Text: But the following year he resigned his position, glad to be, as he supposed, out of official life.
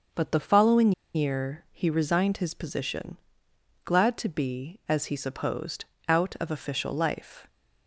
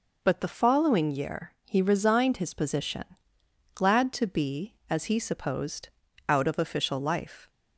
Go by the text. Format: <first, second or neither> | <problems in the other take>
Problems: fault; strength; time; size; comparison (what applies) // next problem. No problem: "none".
second | starts louder than the rest; until 1.3 s; 6 dB // pauses between "following" and "year"; slight; at 0.9 s; 0.23 s long